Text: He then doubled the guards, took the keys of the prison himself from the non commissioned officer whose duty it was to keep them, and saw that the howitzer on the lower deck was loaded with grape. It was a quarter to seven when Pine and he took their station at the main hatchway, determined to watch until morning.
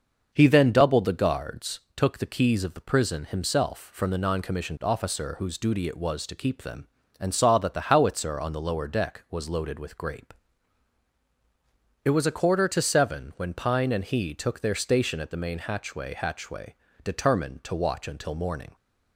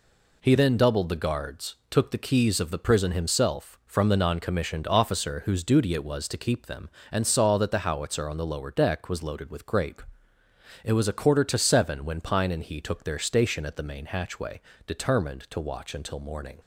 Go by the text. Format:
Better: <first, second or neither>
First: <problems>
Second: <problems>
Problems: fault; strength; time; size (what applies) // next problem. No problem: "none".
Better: second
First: starts louder than the rest; until 1.3 s; 6 dB // says "hatchway" twice; at 16.1 s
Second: none